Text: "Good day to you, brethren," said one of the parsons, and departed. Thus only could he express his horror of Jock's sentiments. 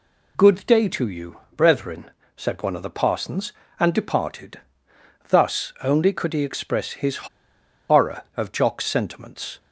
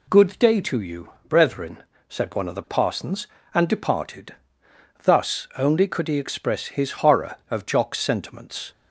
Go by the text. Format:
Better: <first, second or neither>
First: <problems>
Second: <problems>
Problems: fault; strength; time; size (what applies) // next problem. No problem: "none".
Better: second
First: pauses between "his" and "horror"; noticeable; at 7.2 s; 0.63 s long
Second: none